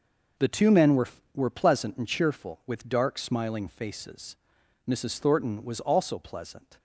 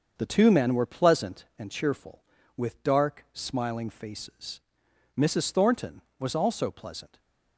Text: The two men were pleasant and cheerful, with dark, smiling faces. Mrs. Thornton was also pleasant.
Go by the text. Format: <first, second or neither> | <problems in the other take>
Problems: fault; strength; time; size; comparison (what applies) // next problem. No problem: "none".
second | starts louder than the rest; until 1.6 s; 7 dB; also in the second // says "were" twice; at 1.3 s